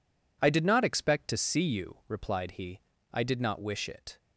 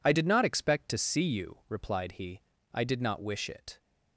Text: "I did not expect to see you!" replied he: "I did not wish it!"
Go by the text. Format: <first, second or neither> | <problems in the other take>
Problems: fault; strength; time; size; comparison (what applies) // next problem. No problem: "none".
neither | none